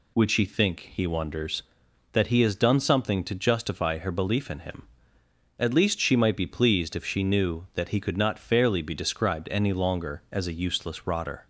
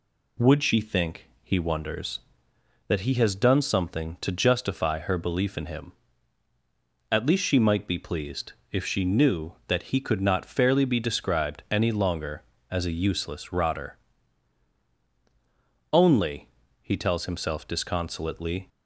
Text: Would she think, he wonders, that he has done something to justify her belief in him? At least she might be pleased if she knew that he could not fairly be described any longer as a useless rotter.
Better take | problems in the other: first | pauses between "pleased" and "if"; slight; at 8.5 s; 0.18 s long // goes on to say "Only he tells himself disconsolately"; strong; from 15.9 s on; 2.7 s long

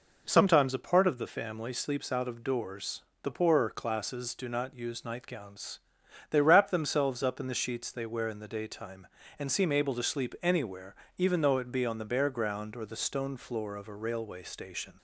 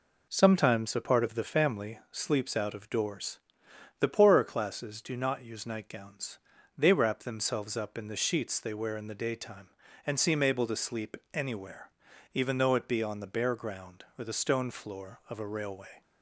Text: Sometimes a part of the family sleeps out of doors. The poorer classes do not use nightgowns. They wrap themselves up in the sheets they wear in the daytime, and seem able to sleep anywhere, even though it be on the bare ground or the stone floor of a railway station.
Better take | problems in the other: first | pauses between "sleep" and "anywhere"; slight; at 11.1 s; 0.16 s long // stops before "station"; at 16.0 s

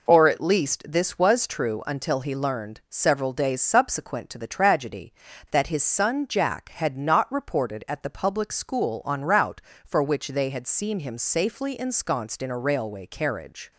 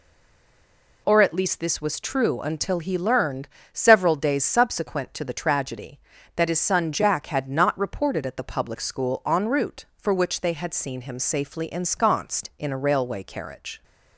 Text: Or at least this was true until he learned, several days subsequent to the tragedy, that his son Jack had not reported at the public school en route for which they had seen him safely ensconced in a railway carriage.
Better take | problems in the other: first | stays silent before the first word; until 1.0 s; 1.0 s long

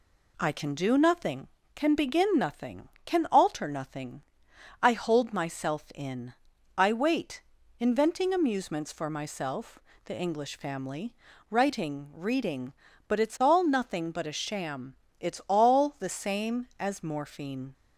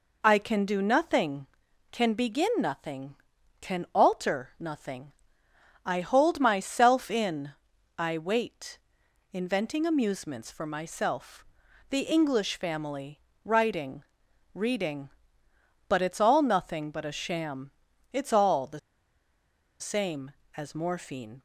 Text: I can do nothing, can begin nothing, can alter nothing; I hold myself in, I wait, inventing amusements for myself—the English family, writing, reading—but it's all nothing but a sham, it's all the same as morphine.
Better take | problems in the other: first | pauses between "the" and "same"; at 18.7 s; 1.0 s long

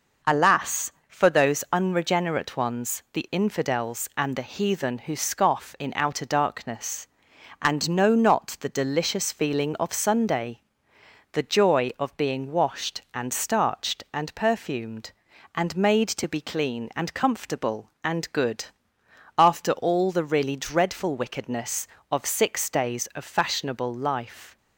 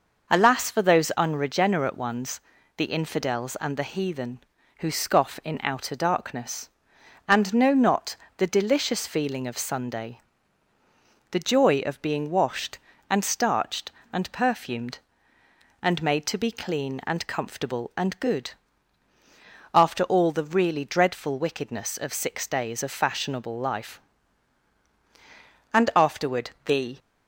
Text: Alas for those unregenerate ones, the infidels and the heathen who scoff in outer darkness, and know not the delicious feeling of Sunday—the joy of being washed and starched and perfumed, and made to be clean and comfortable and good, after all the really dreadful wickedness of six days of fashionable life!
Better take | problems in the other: first | pauses between "not" and "the"; slight; at 8.1 s; 0.22 s long // goes on to say "And afterward the"; noticeable; from 25.7 s on; 1.2 s long

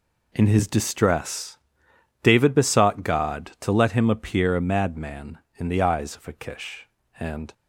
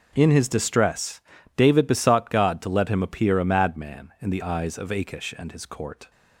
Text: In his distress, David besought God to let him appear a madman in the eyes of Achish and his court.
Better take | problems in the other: second | stops before "his court"; at 7.5 s

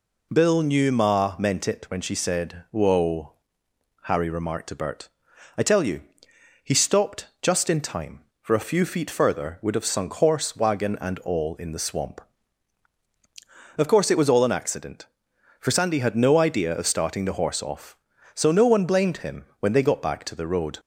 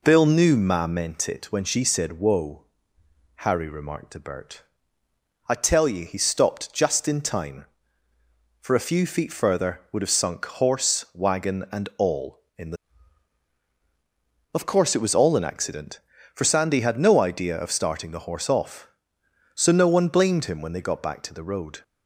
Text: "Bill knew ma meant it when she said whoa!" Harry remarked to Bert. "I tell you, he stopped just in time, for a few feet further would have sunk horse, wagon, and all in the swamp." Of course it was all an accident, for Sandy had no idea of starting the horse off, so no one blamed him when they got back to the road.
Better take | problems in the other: first | skips "swamp"; at 13.6 s

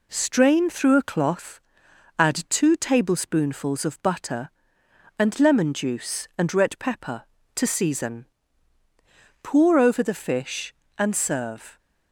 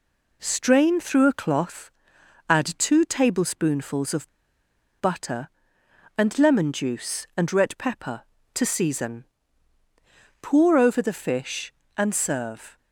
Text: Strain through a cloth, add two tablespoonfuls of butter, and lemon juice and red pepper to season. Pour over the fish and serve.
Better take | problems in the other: first | pauses between "of" and "butter"; noticeable; at 4.2 s; 0.71 s long

